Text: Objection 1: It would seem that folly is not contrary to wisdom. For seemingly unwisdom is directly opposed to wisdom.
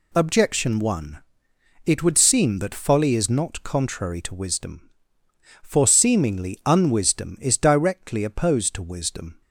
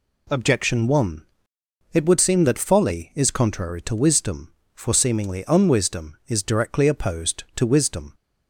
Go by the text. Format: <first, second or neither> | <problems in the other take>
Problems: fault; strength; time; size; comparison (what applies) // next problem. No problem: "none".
first | skips "not"; at 3.2 s